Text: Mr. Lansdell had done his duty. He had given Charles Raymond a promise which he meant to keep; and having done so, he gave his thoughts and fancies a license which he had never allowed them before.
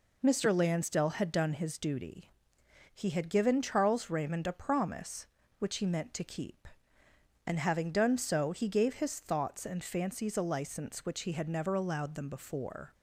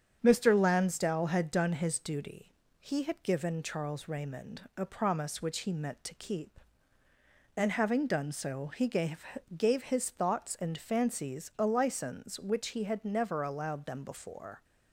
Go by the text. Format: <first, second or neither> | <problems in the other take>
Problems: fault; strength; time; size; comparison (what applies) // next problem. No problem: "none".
first | starts louder than the rest; strong; until 1.2 s; 7.5 dB // says "gave" twice; at 9.5 s